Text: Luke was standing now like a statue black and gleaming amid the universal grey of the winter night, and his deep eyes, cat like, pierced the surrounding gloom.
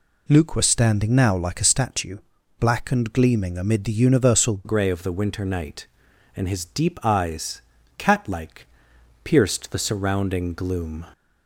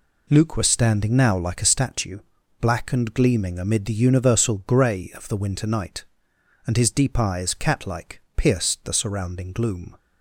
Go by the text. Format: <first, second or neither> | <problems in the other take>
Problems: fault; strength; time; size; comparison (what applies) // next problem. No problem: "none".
second | pauses between "statue" and "black"; at 2.1 s; 0.40 s long; also in the second // changes voice at "grey"; from 4.6 s on; 6.4 s long